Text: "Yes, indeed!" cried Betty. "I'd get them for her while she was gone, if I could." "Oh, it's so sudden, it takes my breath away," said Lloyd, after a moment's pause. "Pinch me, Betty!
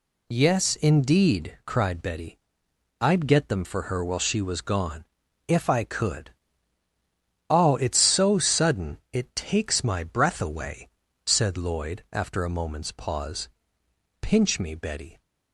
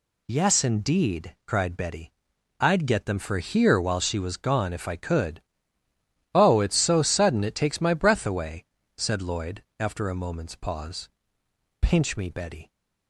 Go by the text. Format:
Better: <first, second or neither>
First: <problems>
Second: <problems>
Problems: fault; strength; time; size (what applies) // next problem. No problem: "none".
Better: first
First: none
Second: says "here" for "her"; at 3.3 s